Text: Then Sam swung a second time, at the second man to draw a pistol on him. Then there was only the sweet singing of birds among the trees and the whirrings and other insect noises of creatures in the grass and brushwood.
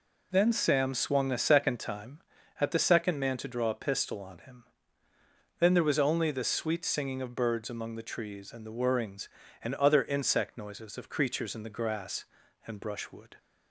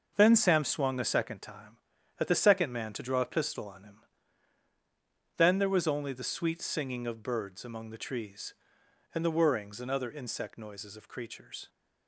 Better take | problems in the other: first | stops before "in the grass and brushwood"; at 11.6 s

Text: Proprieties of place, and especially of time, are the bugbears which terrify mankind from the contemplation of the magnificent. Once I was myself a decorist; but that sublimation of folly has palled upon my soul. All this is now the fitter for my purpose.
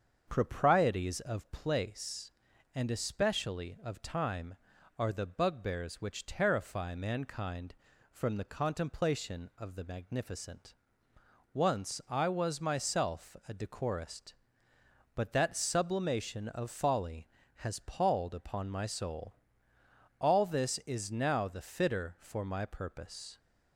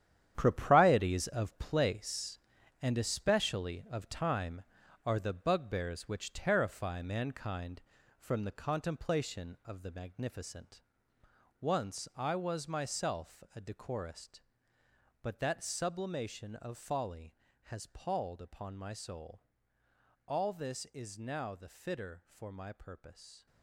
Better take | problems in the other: first | gets quieter; strong; throughout; 10.5 dB // starts louder than the rest; strong; until 1.3 s; 10 dB; also in the first

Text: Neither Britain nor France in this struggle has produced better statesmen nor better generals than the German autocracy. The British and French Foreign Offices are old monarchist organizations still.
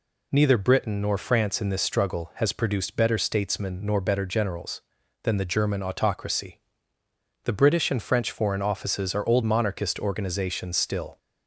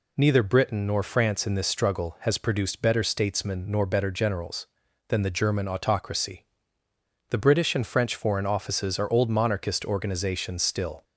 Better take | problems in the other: neither | none

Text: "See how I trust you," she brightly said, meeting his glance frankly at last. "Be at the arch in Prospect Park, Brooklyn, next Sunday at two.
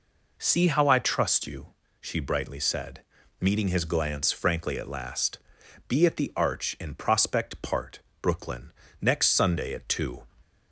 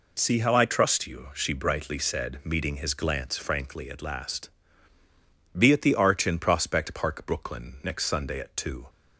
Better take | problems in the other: second | says "Part" for "Park"; at 7.5 s

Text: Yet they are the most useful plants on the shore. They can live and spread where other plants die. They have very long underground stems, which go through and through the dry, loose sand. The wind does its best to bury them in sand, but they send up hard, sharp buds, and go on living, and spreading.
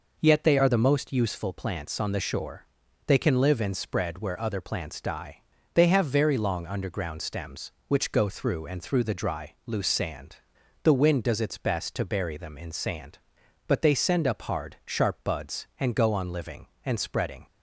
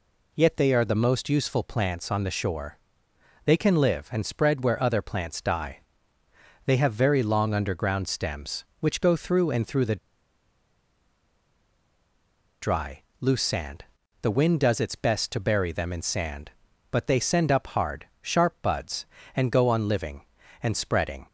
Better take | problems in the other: first | pauses between "the" and "dry"; strong; at 9.9 s; 2.6 s long

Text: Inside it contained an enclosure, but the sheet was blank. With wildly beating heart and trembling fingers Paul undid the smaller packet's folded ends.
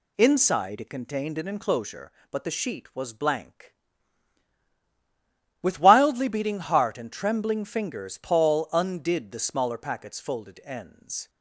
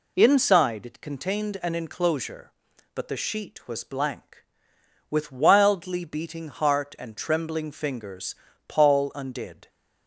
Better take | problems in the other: first | pauses between "fingers" and "Paul"; slight; at 8.3 s; 0.34 s long // stops before "the smaller packet's folded ends"; at 9.6 s

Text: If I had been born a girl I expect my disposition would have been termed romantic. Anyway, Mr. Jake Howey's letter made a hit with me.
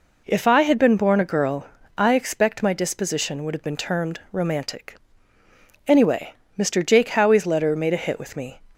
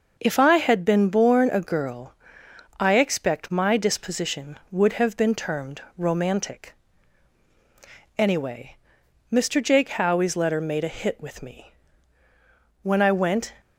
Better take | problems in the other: first | pauses between "girl" and "I"; noticeable; at 2.1 s; 0.66 s long; slight in the first // pauses between "termed" and "romantic"; slight; at 5.8 s; 0.16 s long // goes on to say "When I went"; noticeable; from 12.8 s on; 0.70 s long

